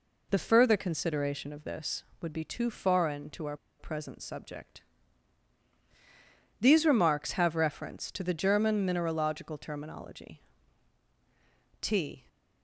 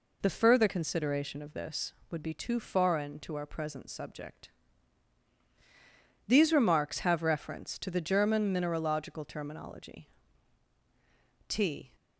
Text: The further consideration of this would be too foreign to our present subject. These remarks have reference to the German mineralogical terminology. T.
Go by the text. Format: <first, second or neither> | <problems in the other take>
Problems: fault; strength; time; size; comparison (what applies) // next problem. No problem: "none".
second | pauses between "our" and "present"; slight; at 3.5 s; 0.23 s long